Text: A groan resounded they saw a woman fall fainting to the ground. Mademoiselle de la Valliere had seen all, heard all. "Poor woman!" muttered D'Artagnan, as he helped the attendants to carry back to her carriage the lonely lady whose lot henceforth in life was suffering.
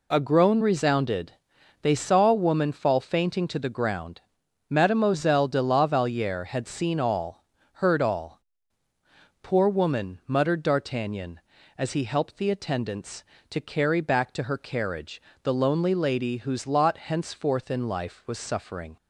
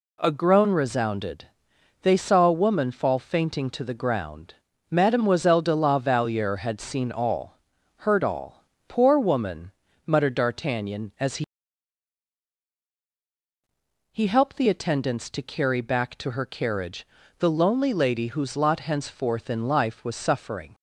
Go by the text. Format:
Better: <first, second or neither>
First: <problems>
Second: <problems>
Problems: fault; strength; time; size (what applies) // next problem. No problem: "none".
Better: first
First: pauses between "resounded" and "they"; noticeable; at 1.3 s; 0.48 s long // pauses between "carriage" and "the"; slight; at 15.2 s; 0.22 s long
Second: pauses between "resounded" and "they"; noticeable; at 1.4 s; 0.56 s long // says "he" twice; at 14.1 s // pauses between "carriage" and "the"; slight; at 17.0 s; 0.32 s long